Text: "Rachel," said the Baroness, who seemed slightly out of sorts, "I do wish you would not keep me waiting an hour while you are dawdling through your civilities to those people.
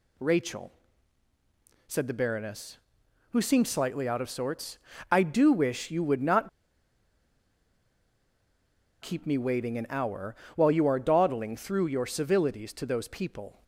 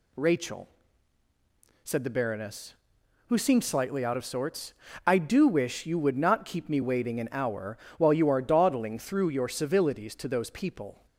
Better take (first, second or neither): second